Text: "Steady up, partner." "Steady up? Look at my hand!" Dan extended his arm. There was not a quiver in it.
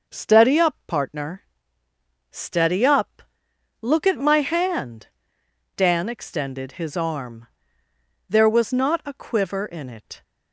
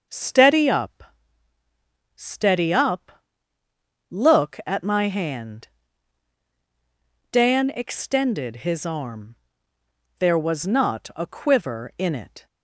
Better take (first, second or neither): first